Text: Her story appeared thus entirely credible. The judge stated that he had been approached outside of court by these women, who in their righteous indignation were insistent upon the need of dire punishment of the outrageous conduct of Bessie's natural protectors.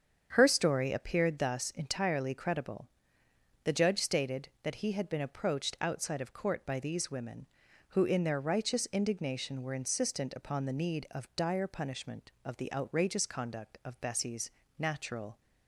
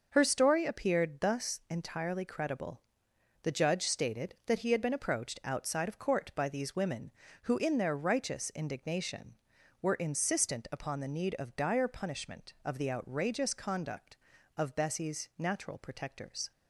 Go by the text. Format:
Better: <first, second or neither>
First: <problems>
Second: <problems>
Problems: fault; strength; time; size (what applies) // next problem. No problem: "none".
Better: second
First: starts louder than the rest; strong; until 1.3 s; 7.5 dB // pauses between "Bessie's" and "natural"; slight; at 14.5 s; 0.26 s long // stops before "protectors"; at 15.3 s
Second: none